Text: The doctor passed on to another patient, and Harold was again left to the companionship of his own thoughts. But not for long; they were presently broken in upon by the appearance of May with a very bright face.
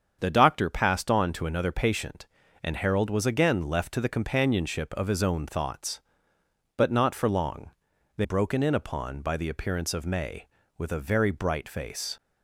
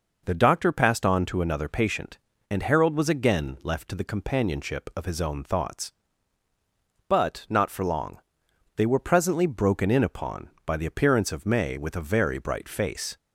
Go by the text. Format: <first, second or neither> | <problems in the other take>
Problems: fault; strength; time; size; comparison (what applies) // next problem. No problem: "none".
second | starts louder than the rest; strong; until 1.2 s; 7.5 dB // skips "were presently"; at 8.2 s